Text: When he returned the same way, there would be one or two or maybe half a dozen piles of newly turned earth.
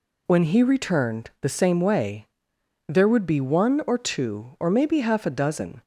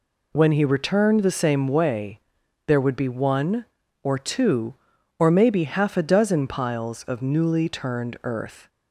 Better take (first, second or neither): second